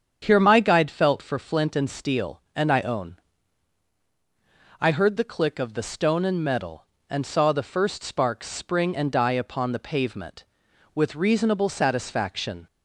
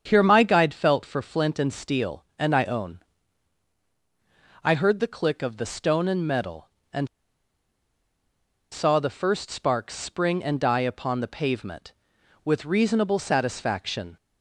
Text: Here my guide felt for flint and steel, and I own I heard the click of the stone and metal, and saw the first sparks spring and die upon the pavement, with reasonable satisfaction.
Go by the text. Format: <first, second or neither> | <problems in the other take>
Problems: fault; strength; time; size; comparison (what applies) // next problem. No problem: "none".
first | starts louder than the rest; strong; until 1.0 s; 7.5 dB; strong in the first // pauses between "own" and "I"; strong; at 3.0 s; 1.6 s long; strong in the first // pauses between "and" and "saw"; strong; at 7.0 s; 1.6 s long